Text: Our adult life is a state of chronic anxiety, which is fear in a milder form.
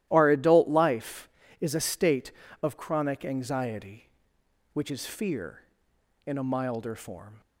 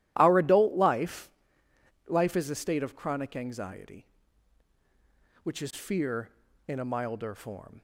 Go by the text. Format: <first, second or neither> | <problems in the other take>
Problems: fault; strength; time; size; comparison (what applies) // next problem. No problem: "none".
first | starts louder than the rest; strong; until 1.1 s; 13.5 dB; strong in the first // says "life" twice; at 2.0 s